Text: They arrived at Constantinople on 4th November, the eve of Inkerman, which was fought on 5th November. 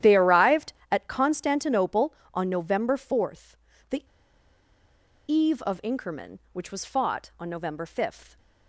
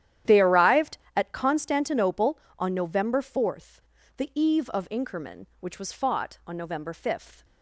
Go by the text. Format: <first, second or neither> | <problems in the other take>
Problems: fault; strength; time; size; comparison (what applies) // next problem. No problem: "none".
second | starts louder than the rest; strong; until 1.1 s; 11 dB; strong in the second // pauses between "the" and "eve"; at 4.0 s; 1.2 s long